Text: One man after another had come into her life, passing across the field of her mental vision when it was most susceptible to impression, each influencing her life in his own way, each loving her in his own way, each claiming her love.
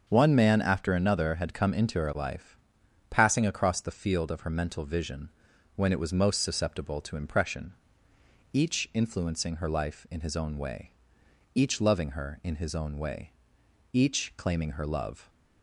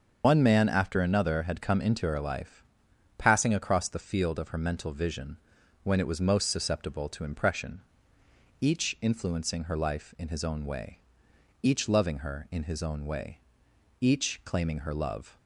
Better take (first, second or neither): first